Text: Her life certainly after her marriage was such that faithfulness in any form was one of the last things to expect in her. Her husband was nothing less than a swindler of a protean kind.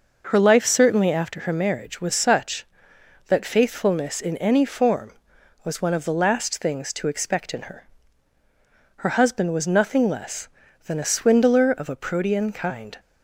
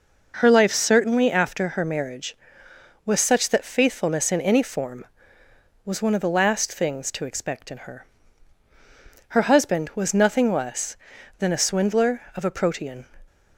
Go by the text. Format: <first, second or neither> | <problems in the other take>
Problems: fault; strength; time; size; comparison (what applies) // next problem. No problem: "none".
first | stops before "kind"; at 13.2 s